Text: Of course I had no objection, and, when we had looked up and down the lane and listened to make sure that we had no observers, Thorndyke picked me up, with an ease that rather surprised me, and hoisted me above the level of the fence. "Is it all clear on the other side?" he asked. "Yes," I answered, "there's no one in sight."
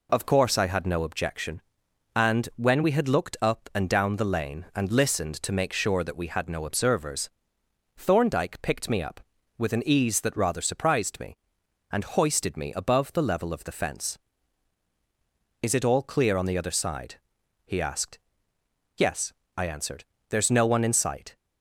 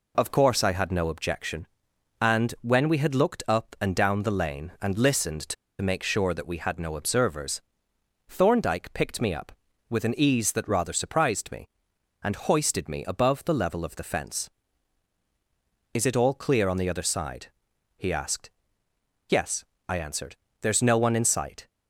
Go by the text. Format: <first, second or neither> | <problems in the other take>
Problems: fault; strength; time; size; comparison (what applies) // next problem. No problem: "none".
first | pauses between "to" and "make"; slight; at 5.5 s; 0.26 s long